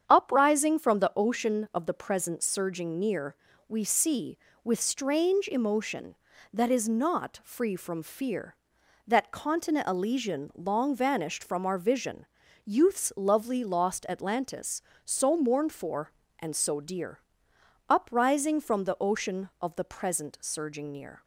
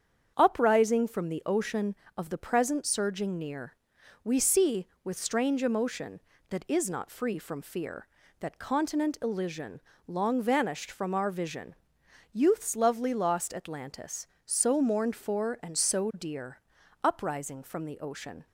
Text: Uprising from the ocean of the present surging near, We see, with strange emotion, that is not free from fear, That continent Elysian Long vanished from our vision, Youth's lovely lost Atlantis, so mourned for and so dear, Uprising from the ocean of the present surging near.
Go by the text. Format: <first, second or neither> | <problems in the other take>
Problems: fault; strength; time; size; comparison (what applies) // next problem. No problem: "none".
first | starts louder than the rest; strong; until 1.3 s; 8 dB; strong in the first // pauses between "Elysian" and "Long"; slight; at 9.7 s; 0.28 s long // stops before "of the present surging near"; at 18.4 s